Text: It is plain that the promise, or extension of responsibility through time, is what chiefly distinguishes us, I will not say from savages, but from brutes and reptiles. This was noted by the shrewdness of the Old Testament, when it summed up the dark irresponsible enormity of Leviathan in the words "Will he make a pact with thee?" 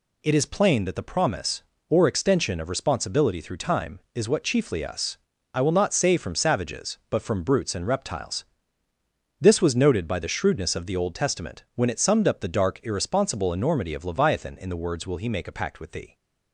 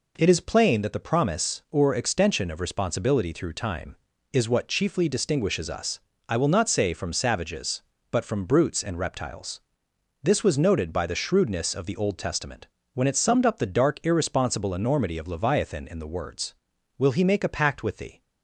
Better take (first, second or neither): second